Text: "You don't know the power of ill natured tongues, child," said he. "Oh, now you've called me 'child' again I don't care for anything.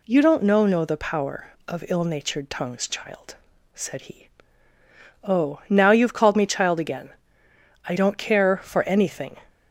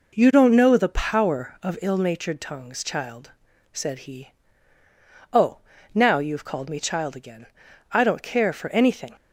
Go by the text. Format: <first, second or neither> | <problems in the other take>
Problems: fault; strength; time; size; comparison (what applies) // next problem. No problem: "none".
second | says "know" twice; at 0.6 s // pauses between "again" and "I"; noticeable; at 7.1 s; 0.74 s long; also in the second